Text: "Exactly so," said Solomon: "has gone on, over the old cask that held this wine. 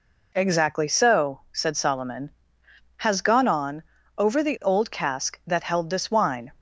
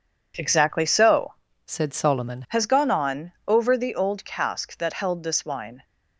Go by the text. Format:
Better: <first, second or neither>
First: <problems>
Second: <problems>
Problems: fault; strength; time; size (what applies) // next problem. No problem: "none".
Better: first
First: none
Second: changes voice from "said" to "Solomon"; from 1.6 to 2.4 s; 0.8 s long